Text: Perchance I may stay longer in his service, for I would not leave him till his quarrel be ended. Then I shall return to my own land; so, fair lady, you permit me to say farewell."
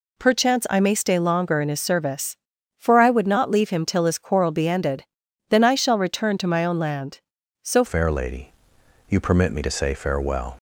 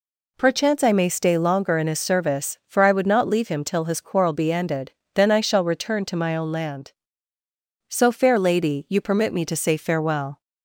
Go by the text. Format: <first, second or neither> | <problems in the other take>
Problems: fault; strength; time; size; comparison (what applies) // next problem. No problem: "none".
second | changes voice at "fair"; from 7.8 s on; 2.7 s long